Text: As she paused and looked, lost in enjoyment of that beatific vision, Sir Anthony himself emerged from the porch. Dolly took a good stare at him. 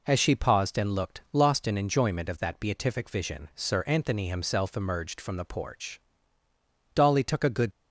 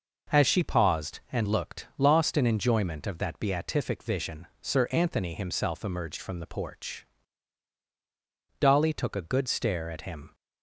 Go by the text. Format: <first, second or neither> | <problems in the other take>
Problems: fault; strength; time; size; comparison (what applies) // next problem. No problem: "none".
second | stops before "stare at him"; at 7.7 s